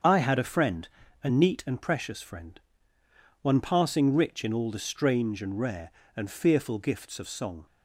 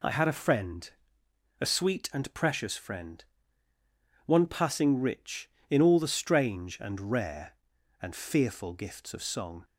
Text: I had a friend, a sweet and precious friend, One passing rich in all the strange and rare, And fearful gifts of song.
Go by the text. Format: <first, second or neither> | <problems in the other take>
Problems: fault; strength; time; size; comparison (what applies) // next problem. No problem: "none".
second | starts louder than the rest; strong; until 1.3 s; 7 dB // says "neat" for "sweet"; at 1.2 s